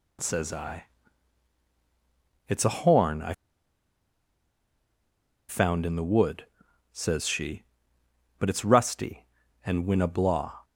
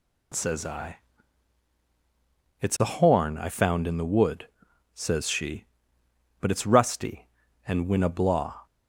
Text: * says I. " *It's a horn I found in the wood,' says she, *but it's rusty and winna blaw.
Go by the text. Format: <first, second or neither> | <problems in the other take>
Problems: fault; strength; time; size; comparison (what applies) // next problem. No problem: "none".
second | pauses between "I" and "found"; strong; at 3.3 s; 2.1 s long